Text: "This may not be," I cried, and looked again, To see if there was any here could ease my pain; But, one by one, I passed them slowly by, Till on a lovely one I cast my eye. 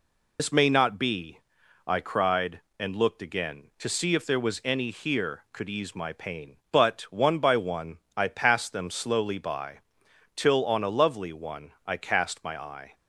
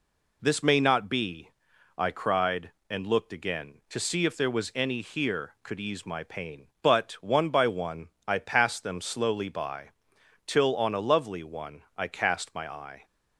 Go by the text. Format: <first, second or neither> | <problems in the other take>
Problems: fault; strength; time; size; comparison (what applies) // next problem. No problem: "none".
second | loses the start of "This"; at 0.3 s; 90 ms